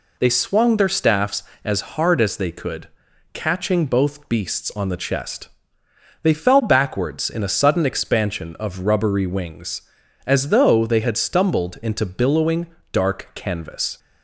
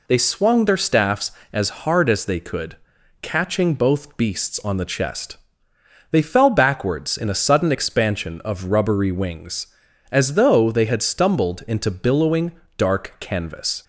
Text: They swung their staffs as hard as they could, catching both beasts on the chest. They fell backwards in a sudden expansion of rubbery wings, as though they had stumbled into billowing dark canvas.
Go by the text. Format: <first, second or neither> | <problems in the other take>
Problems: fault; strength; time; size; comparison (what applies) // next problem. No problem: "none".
neither | pauses between "billowing" and "dark"; slight; the same in both